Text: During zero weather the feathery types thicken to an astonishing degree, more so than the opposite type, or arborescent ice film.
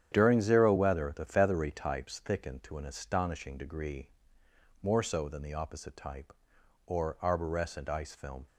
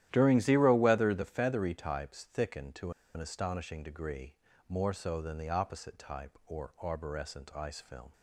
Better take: first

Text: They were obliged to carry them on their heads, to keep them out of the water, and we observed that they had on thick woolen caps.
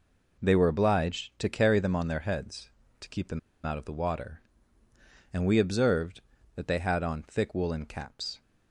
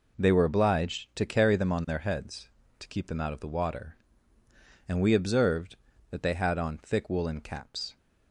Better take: second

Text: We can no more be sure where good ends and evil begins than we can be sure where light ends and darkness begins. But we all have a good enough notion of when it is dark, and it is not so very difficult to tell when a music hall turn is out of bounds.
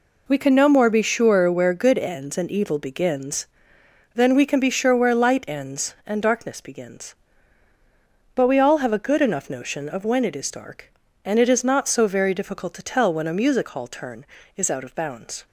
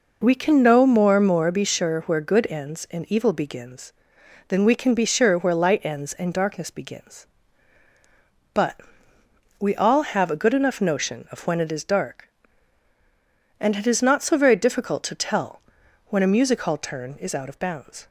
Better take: first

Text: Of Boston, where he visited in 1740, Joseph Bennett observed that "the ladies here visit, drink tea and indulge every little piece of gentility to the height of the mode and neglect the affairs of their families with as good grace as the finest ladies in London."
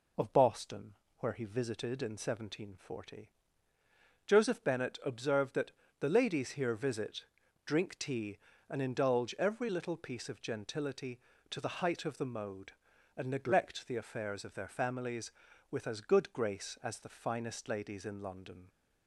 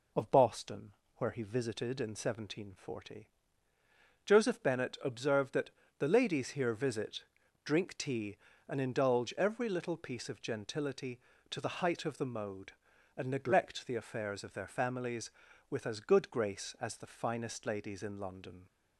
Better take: neither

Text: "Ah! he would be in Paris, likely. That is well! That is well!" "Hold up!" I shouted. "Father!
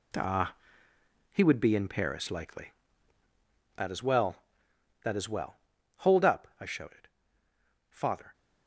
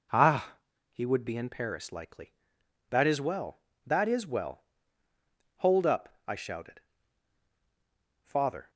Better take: second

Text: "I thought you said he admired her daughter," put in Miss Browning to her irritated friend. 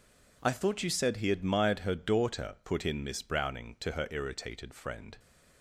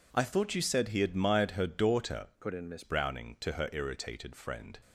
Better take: first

